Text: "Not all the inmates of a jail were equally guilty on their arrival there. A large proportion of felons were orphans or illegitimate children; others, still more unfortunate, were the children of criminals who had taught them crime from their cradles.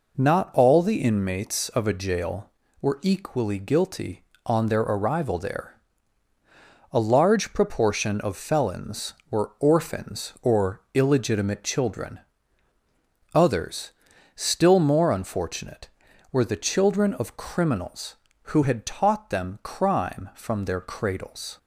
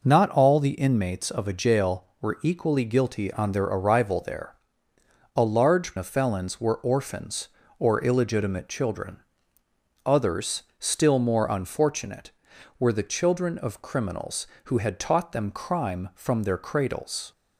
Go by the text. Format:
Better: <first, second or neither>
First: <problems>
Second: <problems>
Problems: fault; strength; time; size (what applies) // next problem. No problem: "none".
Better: first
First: none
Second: skips "proportion"; at 5.9 s